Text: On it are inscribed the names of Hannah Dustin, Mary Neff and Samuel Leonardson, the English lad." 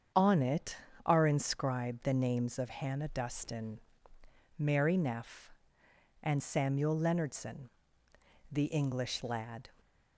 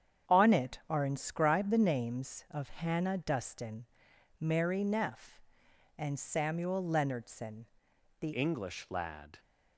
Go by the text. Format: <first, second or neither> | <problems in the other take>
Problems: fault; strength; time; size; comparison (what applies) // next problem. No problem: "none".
first | starts louder than the rest; strong; until 1.4 s; 8.5 dB; strong in the first // changes voice at "English"; from 8.3 s on; 1.0 s long